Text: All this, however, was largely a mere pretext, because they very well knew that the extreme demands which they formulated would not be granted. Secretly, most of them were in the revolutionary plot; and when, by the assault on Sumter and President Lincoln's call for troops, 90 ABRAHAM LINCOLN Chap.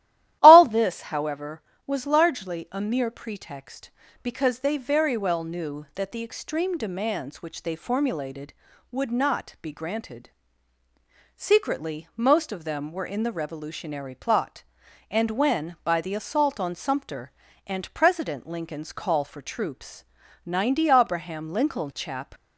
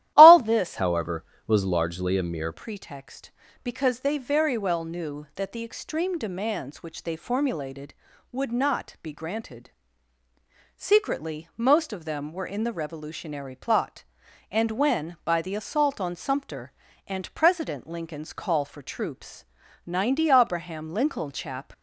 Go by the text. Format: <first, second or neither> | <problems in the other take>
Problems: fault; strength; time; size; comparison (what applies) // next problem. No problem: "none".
first | starts louder than the rest; strong; until 1.1 s; 14 dB; strong in the first // changes voice from "however" to "mere"; from 0.7 to 2.5 s; 1.8 s long